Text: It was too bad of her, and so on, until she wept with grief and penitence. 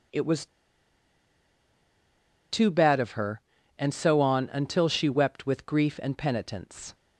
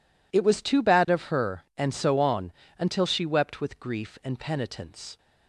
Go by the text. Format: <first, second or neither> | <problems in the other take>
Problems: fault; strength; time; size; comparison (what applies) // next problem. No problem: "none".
second | pauses between "was" and "too"; strong; at 0.4 s; 2.0 s long